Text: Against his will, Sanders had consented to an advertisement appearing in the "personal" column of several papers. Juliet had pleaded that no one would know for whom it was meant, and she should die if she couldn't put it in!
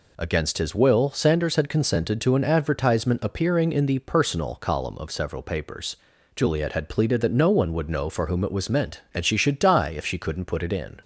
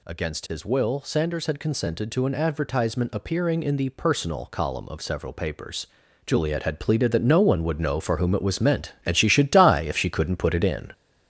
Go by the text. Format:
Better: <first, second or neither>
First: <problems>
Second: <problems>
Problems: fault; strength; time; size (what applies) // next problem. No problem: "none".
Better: first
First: none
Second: gets louder; noticeable; throughout; 6 dB